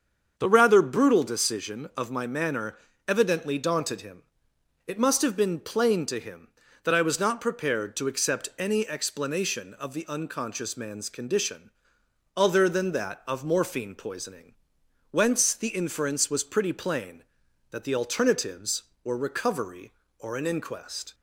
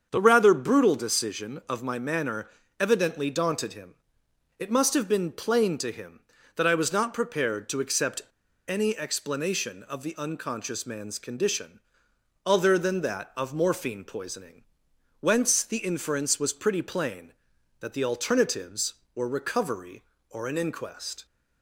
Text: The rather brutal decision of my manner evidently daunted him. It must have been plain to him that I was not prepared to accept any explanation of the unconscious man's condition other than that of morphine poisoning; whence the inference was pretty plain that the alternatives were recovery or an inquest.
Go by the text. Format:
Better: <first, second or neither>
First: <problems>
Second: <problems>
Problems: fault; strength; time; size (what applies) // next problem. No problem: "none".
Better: first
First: starts louder than the rest; strong; until 1.3 s; 7 dB // pauses between "manner" and "evidently"; slight; at 2.7 s; 0.32 s long // pauses between "condition" and "other"; noticeable; at 11.6 s; 0.66 s long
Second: starts louder than the rest; until 1.1 s; 7 dB // pauses between "manner" and "evidently"; slight; at 2.4 s; 0.32 s long // pauses between "accept" and "any"; at 8.2 s; 0.44 s long // pauses between "condition" and "other"; noticeable; at 11.7 s; 0.66 s long